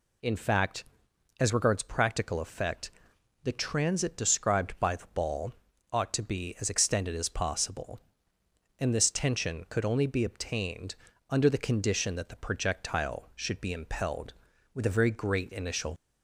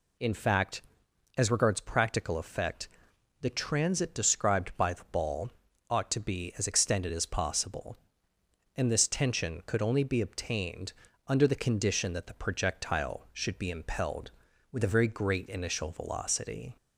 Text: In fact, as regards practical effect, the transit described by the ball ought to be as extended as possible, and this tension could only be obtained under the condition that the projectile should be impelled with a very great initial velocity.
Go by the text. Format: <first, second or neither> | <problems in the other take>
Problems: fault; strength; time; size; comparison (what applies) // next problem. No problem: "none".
second | pauses between "ball" and "ought"; at 5.5 s; 0.38 s long; also in the second // pauses between "obtained" and "under"; slight; at 10.9 s; 0.34 s long; slight in the second // stops before "velocity"; at 15.9 s